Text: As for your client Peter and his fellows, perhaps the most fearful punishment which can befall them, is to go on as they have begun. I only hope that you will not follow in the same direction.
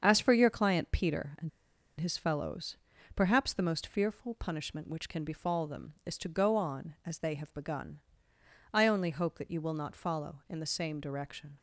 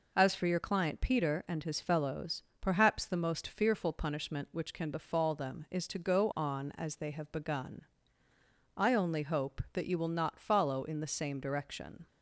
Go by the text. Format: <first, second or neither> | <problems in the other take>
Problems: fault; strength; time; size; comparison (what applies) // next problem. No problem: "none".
second | starts louder than the rest; until 1.0 s; 7 dB // pauses between "and" and "his"; noticeable; at 1.4 s; 0.50 s long